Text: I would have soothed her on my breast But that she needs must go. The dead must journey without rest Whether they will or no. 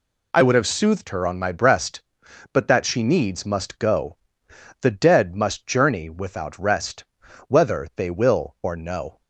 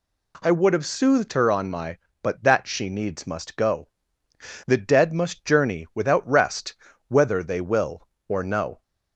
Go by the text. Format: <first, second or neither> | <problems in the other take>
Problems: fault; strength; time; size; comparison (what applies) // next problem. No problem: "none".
first | skips "breast"; at 2.0 s // pauses between "rest" and "Whether"; slight; at 6.7 s; 0.34 s long; also in the first